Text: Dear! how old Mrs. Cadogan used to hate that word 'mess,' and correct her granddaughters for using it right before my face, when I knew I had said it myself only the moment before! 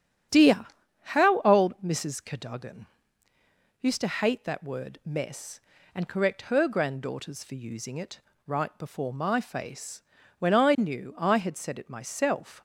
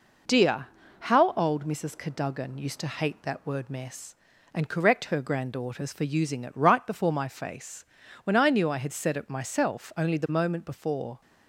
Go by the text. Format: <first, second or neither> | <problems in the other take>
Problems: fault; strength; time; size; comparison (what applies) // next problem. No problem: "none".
second | starts louder than the rest; strong; until 1.7 s; 8.5 dB // pauses between "Cadogan" and "used"; noticeable; at 2.8 s; 0.96 s long // pauses between "it" and "right"; slight; at 8.1 s; 0.26 s long // stops before "only the moment before"; at 12.5 s